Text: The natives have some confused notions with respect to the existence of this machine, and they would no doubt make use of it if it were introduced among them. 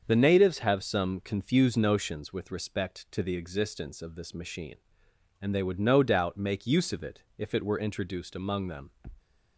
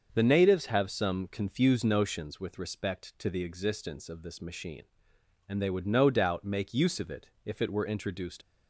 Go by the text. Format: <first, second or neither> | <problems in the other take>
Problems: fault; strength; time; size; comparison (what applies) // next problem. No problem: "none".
first | starts louder than the rest; until 1.1 s; 6.5 dB; also in the first // pauses between "it" and "if"; slight; at 7.2 s; 0.16 s long; slight in the first // stops before "among them"; at 8.4 s